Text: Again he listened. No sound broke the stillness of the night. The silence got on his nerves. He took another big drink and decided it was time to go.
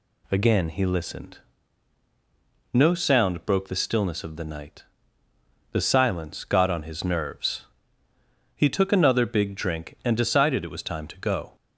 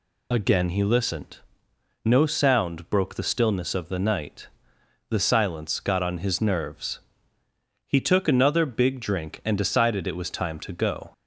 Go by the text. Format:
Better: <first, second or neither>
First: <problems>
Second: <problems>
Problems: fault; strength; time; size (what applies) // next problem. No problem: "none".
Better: first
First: none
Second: loses the start of "Again"; at 0.3 s; 30 ms